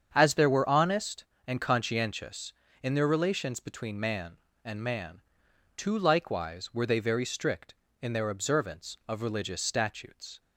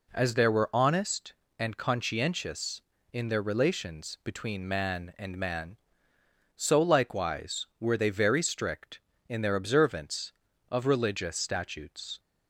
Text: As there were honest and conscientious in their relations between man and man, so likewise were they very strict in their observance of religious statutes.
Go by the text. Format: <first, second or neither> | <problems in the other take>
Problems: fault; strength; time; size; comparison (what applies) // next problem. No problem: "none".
second | starts louder than the rest; strong; until 1.1 s; 7.5 dB // says "too" for "so"; at 5.7 s